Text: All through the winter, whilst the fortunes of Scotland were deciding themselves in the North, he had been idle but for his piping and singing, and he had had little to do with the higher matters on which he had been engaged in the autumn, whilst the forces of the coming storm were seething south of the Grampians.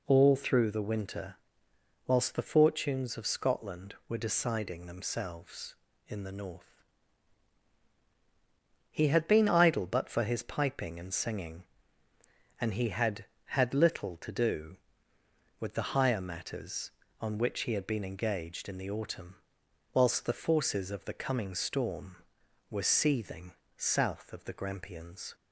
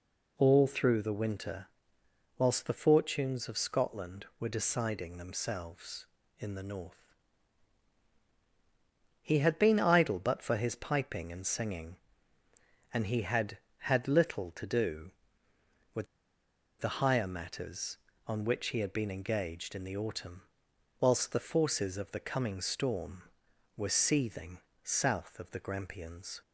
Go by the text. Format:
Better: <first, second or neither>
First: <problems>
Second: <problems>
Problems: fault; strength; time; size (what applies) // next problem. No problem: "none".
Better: first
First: pauses between "seething" and "south"; slight; at 23.5 s; 0.24 s long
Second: pauses between "with" and "the"; noticeable; at 16.0 s; 0.74 s long // pauses between "seething" and "south"; slight; at 24.5 s; 0.24 s long